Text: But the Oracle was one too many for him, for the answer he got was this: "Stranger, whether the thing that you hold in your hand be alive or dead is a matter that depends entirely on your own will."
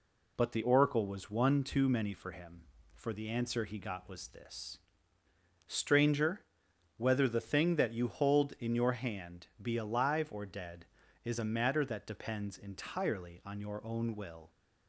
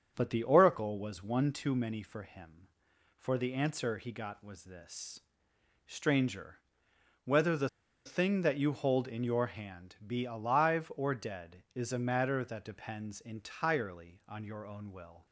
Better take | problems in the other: first | starts louder than the rest; strong; until 1.1 s; 7.5 dB // pauses between "the" and "thing"; at 7.6 s; 0.38 s long

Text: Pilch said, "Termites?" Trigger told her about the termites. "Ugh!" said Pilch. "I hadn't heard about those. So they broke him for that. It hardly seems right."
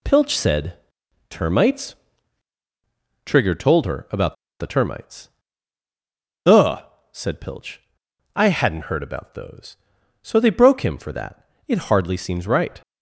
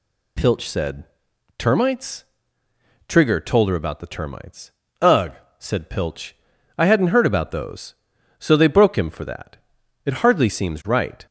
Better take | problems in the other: second | pauses between "about" and "the"; slight; at 4.3 s; 0.25 s long

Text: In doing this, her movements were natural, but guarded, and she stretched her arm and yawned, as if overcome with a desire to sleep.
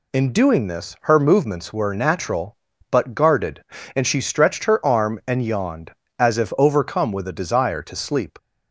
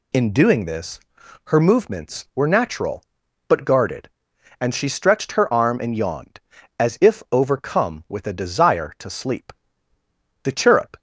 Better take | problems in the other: first | goes on to say "The chirrup"; from 10.4 s on; 0.56 s long

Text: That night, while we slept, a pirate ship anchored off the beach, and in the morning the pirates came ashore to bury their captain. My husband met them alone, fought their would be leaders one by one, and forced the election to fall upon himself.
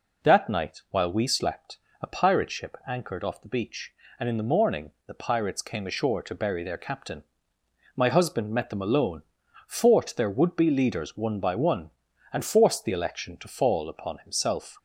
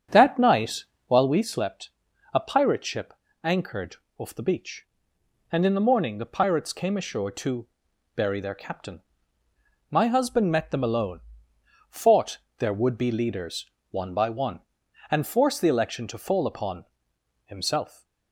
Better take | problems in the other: first | starts louder than the rest; strong; until 1.3 s; 8 dB // pauses between "ship" and "anchored"; slight; at 3.1 s; 0.30 s long // pauses between "anchored" and "off"; slight; at 3.9 s; 0.20 s long // pauses between "to" and "bury"; noticeable; at 7.6 s; 0.48 s long // pauses between "fought" and "their"; slight; at 12.3 s; 0.18 s long // pauses between "leaders" and "one"; slight; at 13.6 s; 0.26 s long // pauses between "upon" and "himself"; noticeable; at 16.8 s; 0.62 s long

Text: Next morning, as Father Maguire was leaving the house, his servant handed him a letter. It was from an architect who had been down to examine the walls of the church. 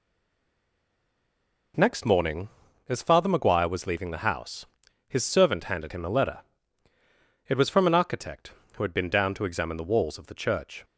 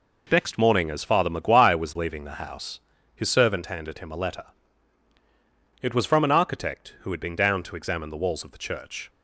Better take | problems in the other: second | stays silent before the first word; noticeable; until 1.7 s; 1.7 s long

